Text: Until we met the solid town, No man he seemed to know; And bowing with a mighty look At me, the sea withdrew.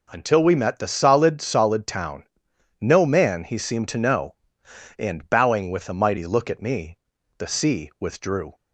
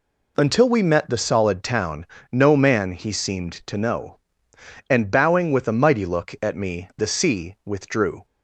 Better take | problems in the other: second | says "solid" twice; at 1.4 s

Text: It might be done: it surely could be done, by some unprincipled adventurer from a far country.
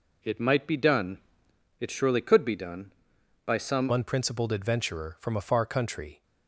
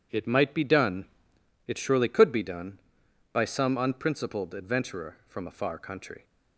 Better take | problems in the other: second | changes voice at "unprincipled"; from 3.9 s on; 2.3 s long

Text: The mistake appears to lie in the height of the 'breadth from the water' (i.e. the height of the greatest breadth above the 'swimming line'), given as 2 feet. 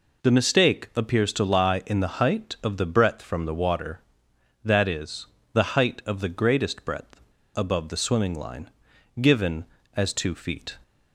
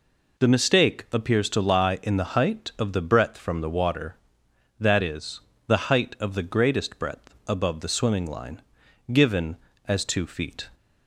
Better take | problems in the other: second | pauses between "breadth" and "above"; at 7.1 s; 0.36 s long

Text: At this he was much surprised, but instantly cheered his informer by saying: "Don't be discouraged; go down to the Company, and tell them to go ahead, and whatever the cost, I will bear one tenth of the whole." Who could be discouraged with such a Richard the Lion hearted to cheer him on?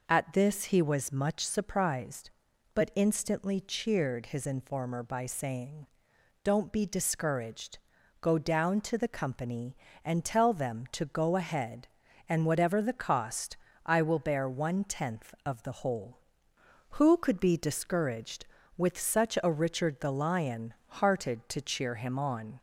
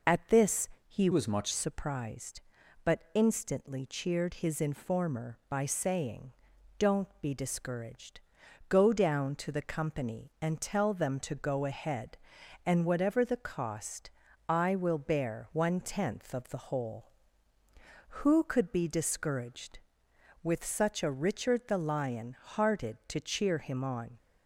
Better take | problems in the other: first | pauses between "this" and "he"; slight; at 0.6 s; 0.20 s long // changes voice from "was" to "much"; from 1.1 to 1.5 s; 0.4 s long

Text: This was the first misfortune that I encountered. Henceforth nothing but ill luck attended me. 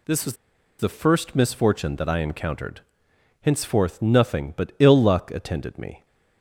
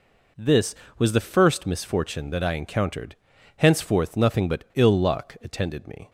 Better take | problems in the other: second | pauses between "was" and "the"; at 0.3 s; 0.44 s long

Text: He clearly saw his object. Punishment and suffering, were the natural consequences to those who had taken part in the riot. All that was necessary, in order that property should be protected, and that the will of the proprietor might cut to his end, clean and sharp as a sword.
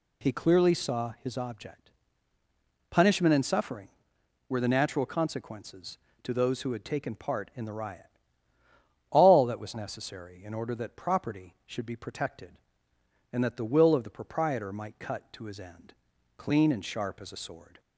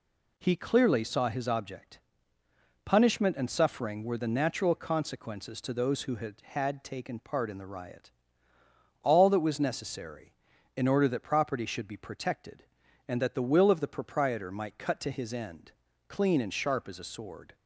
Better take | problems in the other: first | says "had" twice; at 6.4 s

